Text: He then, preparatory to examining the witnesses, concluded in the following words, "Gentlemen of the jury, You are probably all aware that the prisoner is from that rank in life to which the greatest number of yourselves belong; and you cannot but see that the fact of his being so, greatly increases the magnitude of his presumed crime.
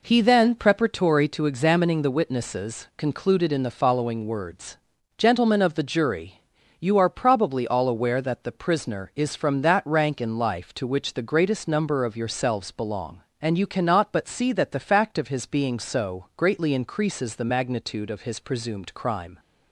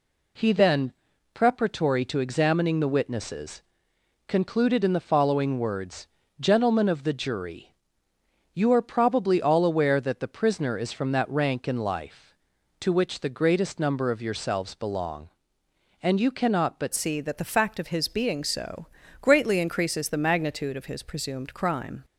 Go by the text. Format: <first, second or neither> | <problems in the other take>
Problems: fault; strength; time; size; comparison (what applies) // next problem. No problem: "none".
first | changes voice at "see"; from 16.9 s on; 5.1 s long